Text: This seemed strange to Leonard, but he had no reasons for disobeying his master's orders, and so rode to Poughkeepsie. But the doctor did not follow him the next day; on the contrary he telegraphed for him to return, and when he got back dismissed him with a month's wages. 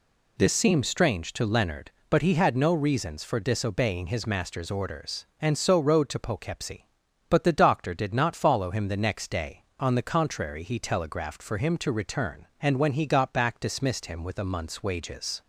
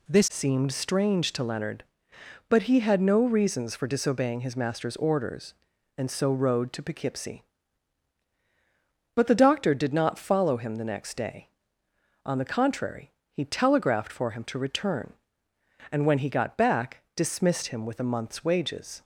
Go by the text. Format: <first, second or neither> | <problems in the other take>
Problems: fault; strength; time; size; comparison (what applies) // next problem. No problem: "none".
first | changes voice at "seemed"; from 0.2 s on; 18.8 s long // pauses between "contrary" and "he"; slight; at 13.1 s; 0.22 s long